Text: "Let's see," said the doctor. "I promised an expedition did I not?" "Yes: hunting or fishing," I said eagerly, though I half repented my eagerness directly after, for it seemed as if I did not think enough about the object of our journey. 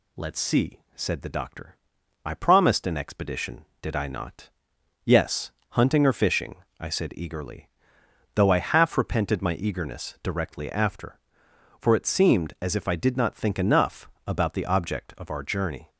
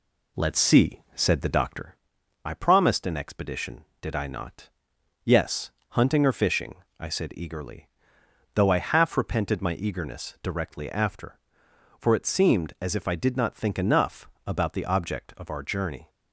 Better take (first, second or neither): first